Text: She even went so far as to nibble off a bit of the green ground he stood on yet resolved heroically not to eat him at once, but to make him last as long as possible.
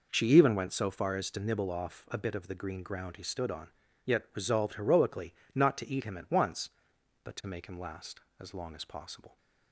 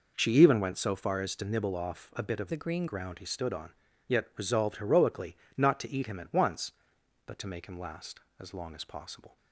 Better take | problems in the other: first | changes voice from "the" to "green"; from 2.4 to 2.8 s; 0.4 s long // pauses between "on" and "yet"; at 3.7 s; 0.38 s long; also in the first // pauses between "heroically" and "not"; slight; at 5.3 s; 0.20 s long; slight in the first

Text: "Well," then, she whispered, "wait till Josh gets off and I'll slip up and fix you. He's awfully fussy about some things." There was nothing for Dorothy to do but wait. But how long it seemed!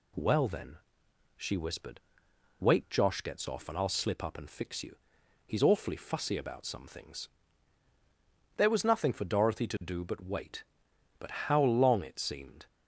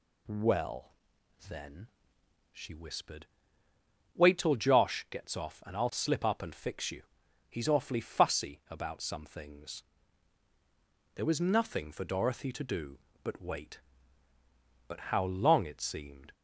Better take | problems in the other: second | skips "till"; at 2.8 s

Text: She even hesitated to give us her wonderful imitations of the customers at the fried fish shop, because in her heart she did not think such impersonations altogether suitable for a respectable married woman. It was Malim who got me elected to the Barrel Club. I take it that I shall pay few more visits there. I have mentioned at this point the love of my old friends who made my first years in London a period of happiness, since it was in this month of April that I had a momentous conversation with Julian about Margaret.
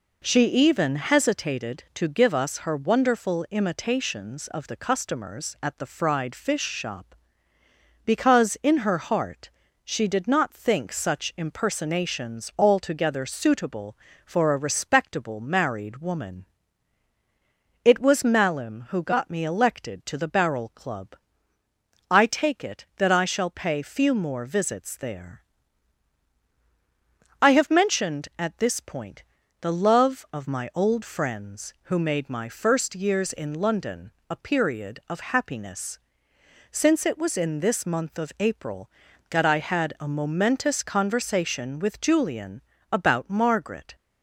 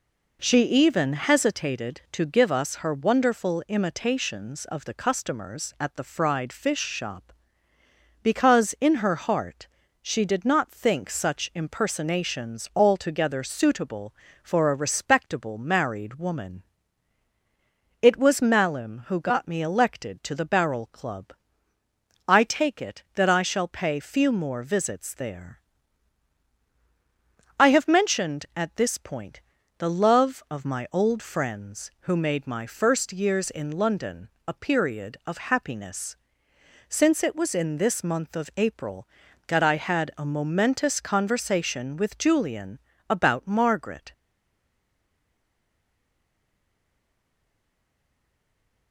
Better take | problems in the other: first | pauses between "heart" and "she"; slight; at 9.6 s; 0.34 s long; slight in the first // pauses between "point" and "the"; slight; at 29.4 s; 0.34 s long; slight in the first // pauses between "London" and "a"; slight; at 34.2 s; 0.18 s long; slight in the first // pauses between "Julian" and "about"; slight; at 42.7 s; 0.30 s long; slight in the first // stays silent after the last word; strong; from 44.1 s on; 4.8 s long

